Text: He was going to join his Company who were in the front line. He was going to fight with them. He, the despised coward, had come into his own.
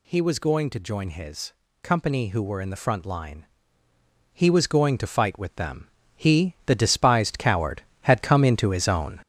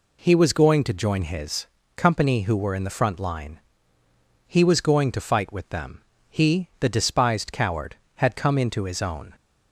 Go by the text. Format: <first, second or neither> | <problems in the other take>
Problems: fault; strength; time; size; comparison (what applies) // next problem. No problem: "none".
second | gets louder; noticeable; throughout; 6 dB // pauses between "his" and "Company"; slight; at 1.5 s; 0.30 s long; slight in the second